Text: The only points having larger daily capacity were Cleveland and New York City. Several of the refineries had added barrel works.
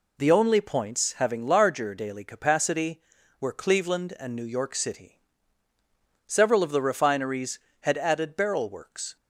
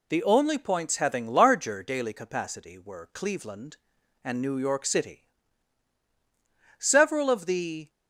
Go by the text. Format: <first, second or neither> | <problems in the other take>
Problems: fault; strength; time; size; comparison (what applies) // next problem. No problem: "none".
first | stops before "refineries had added barrel works"; at 7.8 s